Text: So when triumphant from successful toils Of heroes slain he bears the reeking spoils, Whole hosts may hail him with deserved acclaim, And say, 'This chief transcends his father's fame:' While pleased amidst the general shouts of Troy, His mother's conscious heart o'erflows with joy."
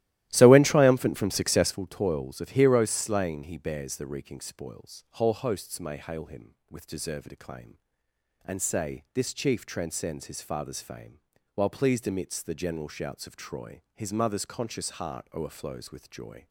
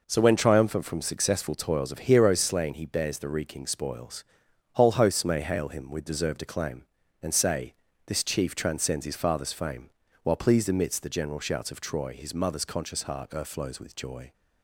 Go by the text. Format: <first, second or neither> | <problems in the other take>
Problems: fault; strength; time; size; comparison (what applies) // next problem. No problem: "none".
second | starts louder than the rest; strong; until 1.8 s; 15 dB